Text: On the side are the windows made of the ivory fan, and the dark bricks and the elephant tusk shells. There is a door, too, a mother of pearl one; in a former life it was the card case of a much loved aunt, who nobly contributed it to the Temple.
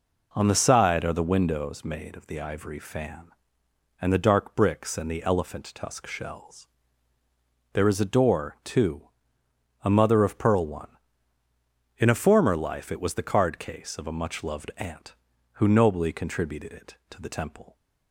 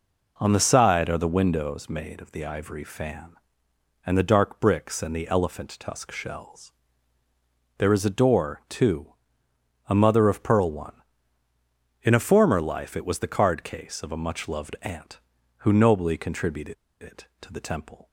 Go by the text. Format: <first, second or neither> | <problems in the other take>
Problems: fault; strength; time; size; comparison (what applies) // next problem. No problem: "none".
first | pauses between "contributed" and "it"; slight; at 16.7 s; 0.26 s long